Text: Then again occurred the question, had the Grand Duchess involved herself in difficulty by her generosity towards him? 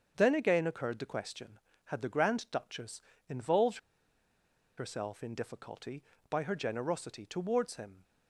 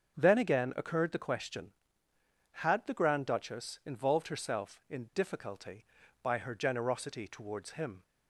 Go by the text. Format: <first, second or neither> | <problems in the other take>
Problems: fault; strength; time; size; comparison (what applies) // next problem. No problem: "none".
second | starts louder than the rest; strong; until 1.1 s; 7 dB; strong in the second // pauses between "Duchess" and "involved"; slight; at 2.9 s; 0.28 s long // pauses between "involved" and "herself"; at 3.7 s; 0.99 s long